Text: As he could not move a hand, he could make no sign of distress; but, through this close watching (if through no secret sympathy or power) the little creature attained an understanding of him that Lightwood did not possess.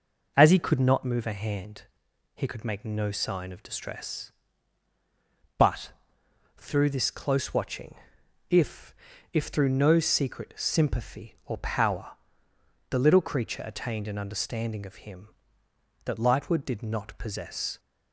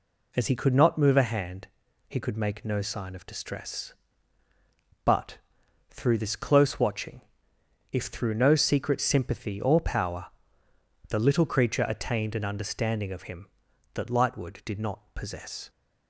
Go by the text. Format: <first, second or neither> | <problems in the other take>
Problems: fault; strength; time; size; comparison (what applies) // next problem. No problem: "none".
second | says "if" twice; at 9.3 s